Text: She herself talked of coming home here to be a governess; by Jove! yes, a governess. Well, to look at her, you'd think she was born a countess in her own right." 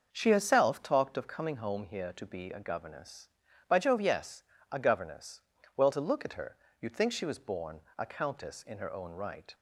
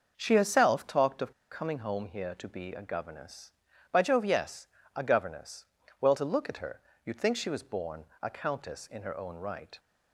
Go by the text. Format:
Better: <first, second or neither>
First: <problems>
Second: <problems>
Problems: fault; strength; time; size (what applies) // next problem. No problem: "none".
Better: first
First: starts louder than the rest; until 1.1 s; 6 dB // pauses between "born" and "a"; slight; at 7.8 s; 0.16 s long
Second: starts louder than the rest; until 1.1 s; 6 dB // pauses between "of" and "coming"; slight; at 1.3 s; 0.18 s long // pauses between "born" and "a"; slight; at 8.0 s; 0.16 s long